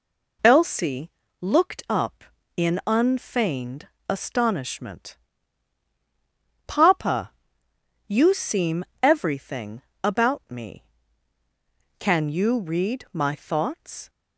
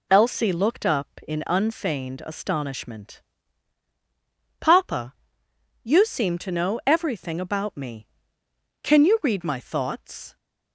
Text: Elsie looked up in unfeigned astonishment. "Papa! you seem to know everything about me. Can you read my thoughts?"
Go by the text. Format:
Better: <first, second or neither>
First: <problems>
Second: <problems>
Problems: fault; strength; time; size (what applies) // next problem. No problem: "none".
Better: second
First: pauses between "Elsie" and "looked"; slight; at 1.0 s; 0.32 s long // pauses between "unfeigned" and "astonishment"; slight; at 3.8 s; 0.18 s long // skips "to know"; at 8.9 s // pauses between "everything" and "about"; slight; at 9.8 s; 0.20 s long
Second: none